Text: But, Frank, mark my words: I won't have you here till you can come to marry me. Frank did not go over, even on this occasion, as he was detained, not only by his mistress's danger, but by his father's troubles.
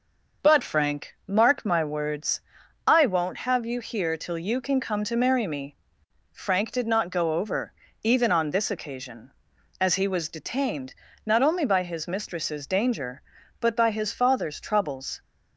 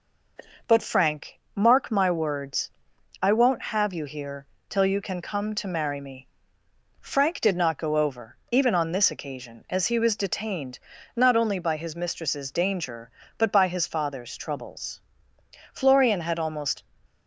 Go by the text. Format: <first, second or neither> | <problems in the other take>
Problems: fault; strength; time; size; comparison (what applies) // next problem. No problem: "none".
first | pauses between "here" and "till"; slight; at 4.4 s; 0.24 s long // goes on to say "Florian had almost"; noticeable; from 15.7 s on; 1.1 s long